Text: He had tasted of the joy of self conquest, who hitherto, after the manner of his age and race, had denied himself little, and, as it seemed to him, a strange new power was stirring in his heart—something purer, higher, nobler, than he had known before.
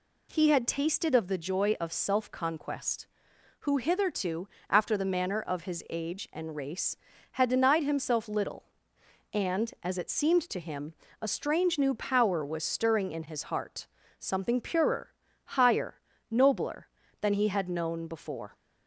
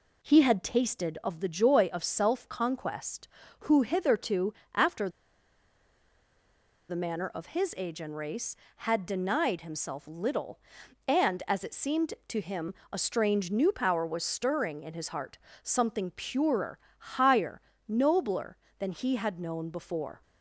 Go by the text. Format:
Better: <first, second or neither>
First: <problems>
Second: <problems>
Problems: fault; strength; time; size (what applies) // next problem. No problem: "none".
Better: first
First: none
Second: pauses between "after" and "the"; strong; at 5.0 s; 1.7 s long